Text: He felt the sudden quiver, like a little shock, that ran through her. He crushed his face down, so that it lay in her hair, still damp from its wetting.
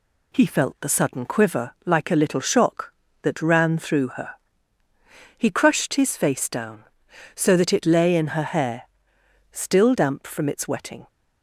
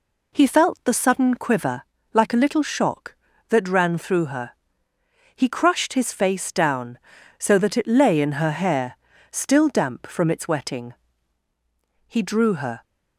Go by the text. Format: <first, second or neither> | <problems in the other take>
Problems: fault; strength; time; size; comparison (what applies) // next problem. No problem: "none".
first | goes on to say "He drew her"; noticeable; from 12.0 s on; 0.76 s long